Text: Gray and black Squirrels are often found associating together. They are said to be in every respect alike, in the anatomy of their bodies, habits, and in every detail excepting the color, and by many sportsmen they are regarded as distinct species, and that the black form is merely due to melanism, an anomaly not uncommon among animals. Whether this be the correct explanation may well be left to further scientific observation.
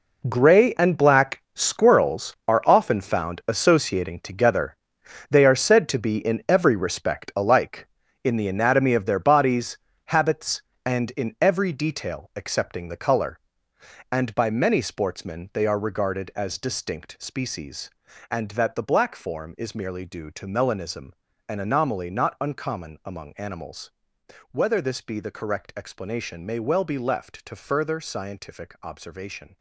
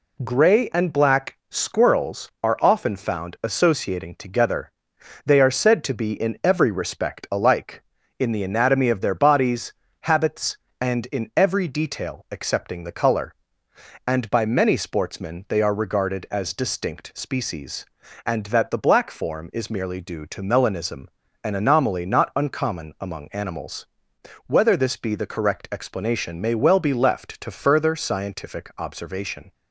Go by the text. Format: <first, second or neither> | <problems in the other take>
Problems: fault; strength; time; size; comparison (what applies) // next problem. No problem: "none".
second | gets quieter; strong; throughout; 12.5 dB